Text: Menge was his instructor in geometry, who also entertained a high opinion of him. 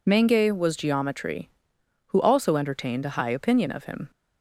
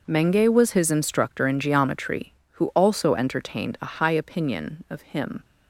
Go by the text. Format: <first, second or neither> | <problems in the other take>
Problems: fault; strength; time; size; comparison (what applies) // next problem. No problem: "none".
second | skips "his instructor in"; at 0.7 s